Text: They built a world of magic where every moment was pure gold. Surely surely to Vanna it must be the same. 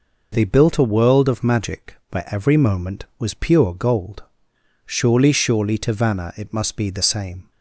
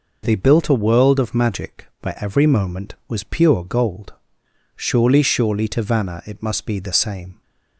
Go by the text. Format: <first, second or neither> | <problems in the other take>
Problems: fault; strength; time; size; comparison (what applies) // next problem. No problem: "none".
neither | none